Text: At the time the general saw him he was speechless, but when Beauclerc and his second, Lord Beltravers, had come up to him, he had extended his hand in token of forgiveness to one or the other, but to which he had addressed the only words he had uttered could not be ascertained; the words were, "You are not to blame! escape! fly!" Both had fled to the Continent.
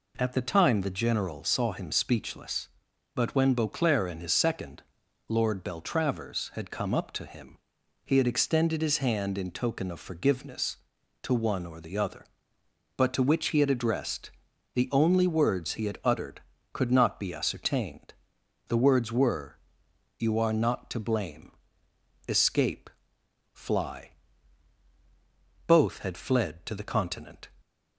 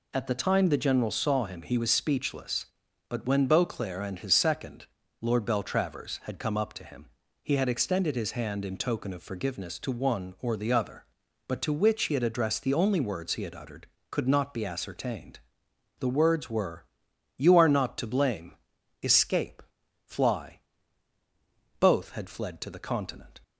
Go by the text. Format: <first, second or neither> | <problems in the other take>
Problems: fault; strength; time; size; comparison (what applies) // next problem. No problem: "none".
second | skips "he was"; at 1.9 s // pauses between "addressed" and "the"; at 14.2 s; 0.44 s long